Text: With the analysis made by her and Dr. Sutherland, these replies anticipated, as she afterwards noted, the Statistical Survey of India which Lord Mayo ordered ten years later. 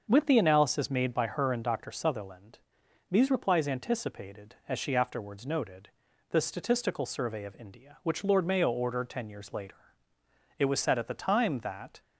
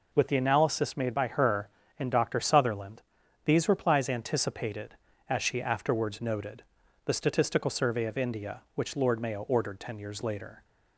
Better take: second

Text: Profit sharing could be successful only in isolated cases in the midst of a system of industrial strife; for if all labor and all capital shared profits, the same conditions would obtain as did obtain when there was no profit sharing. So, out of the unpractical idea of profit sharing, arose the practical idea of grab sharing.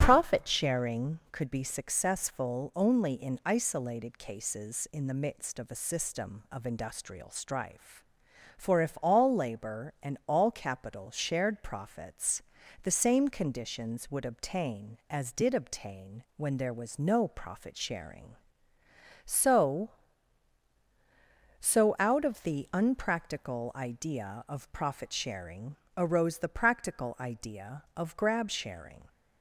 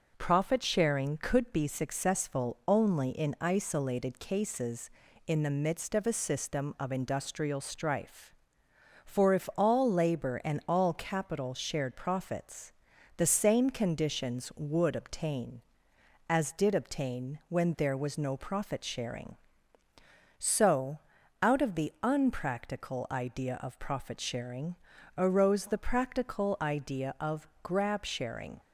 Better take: second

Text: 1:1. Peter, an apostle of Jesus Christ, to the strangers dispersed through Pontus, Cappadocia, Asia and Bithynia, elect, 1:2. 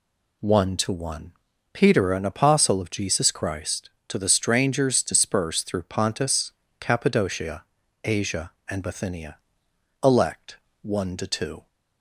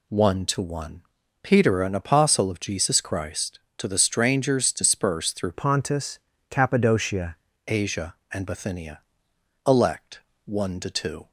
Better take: first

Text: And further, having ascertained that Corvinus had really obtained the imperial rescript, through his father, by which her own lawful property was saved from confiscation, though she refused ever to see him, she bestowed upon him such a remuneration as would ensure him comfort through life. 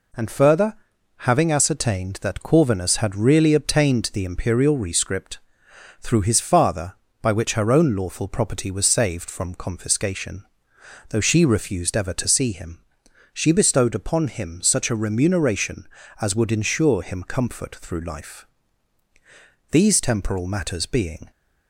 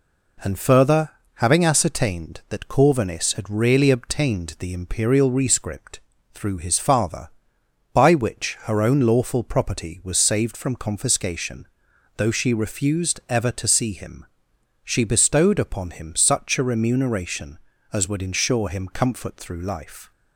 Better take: second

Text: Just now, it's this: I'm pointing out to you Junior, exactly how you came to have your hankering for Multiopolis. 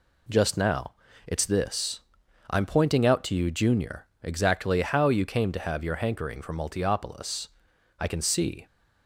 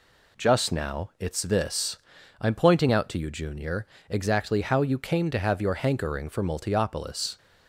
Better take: second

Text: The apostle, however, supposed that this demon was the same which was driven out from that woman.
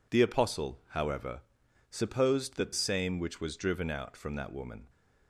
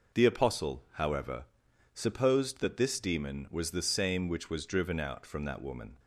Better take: second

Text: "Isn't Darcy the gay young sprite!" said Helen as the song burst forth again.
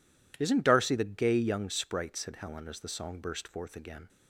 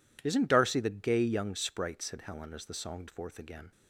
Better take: first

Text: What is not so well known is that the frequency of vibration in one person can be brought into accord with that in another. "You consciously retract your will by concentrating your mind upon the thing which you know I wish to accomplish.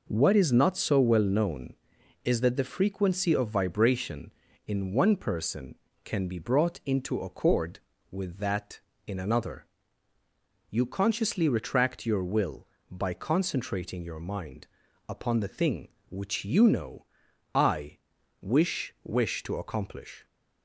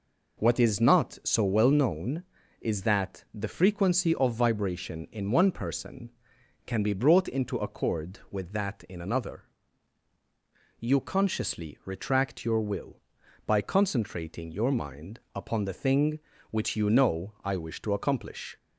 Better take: second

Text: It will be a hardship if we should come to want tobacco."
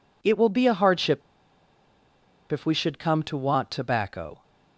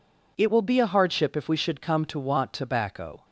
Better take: second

